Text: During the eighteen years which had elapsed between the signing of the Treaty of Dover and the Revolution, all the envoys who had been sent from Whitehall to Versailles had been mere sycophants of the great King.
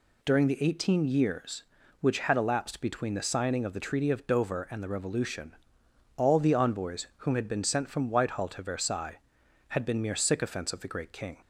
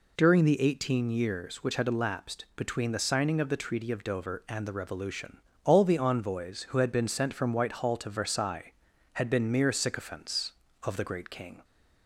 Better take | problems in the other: second | says "whom" for "who"; at 7.1 s

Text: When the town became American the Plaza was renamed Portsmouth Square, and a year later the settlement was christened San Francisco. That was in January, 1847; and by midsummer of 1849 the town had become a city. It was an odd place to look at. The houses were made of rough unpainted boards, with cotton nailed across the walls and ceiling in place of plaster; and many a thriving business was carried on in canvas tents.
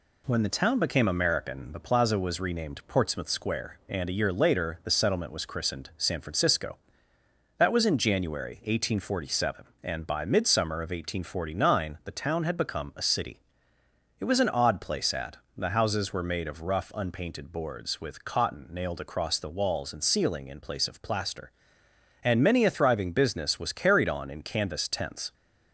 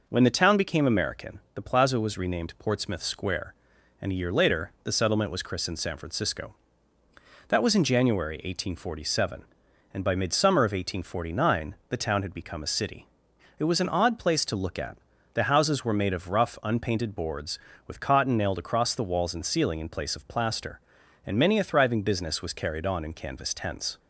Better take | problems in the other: second | skips "to look"; at 15.1 s

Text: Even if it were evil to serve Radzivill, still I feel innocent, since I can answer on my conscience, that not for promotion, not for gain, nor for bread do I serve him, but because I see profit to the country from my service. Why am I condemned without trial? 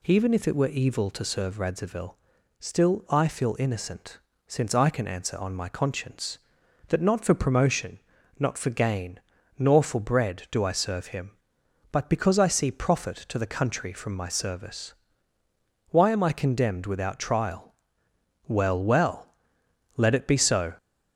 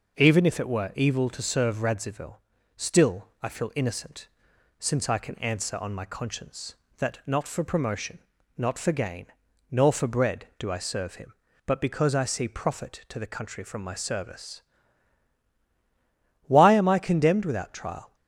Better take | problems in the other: second | goes on to say "Well well Let it be so"; strong; from 18.4 s on; 2.2 s long

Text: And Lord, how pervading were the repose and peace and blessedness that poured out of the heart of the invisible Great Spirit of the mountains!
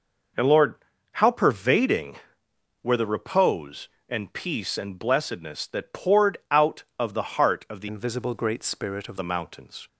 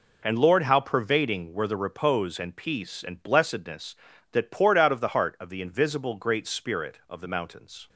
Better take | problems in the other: second | changes voice from "invisible" to "of"; from 7.8 to 9.1 s; 1.3 s long

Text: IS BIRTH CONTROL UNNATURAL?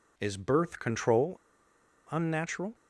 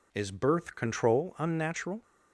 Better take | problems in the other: second | pauses between "CONTROL" and "UNNATURAL"; noticeable; at 1.3 s; 0.72 s long

